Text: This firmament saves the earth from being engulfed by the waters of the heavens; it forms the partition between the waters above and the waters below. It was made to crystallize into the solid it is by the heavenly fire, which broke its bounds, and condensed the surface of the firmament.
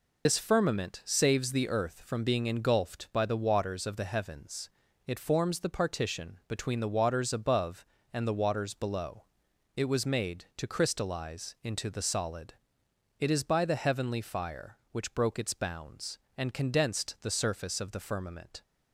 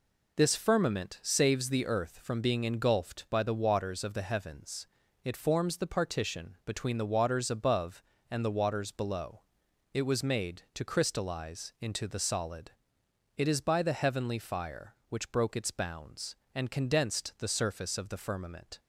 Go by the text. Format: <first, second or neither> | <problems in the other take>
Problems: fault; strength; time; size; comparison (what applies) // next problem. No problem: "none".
second | loses the start of "This"; at 0.2 s; 70 ms // pauses between "solid" and "it"; noticeable; at 12.5 s; 0.64 s long; noticeable in the second